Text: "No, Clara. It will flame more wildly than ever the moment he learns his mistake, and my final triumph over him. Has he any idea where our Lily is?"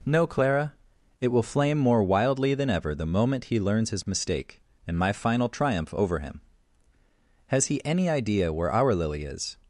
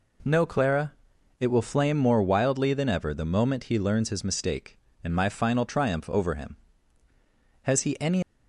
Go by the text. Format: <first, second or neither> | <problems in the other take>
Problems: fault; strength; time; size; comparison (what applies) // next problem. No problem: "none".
first | stops before "idea where our Lily is"; at 8.2 s